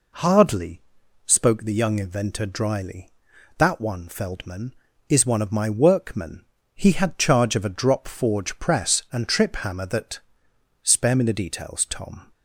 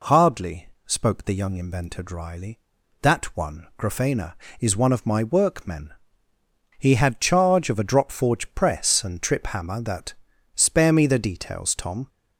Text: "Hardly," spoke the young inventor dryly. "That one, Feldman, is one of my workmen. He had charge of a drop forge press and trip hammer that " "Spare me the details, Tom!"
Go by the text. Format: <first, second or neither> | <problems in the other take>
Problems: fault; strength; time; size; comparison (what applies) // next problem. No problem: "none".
first | says "Grafena" for "Feldman"; at 3.7 s